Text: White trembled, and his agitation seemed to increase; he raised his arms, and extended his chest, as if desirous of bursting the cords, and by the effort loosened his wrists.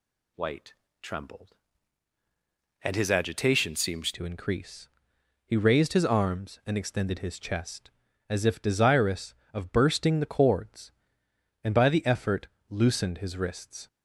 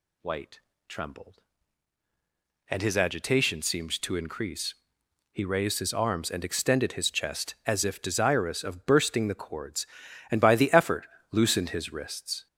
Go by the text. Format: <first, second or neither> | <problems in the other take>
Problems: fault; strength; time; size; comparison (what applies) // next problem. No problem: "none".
second | pauses between "White" and "trembled"; slight; at 0.7 s; 0.28 s long; slight in the second // changes voice at "to"; from 4.1 s on; 9.7 s long // pauses between "effort" and "loosened"; slight; at 12.4 s; 0.22 s long; slight in the second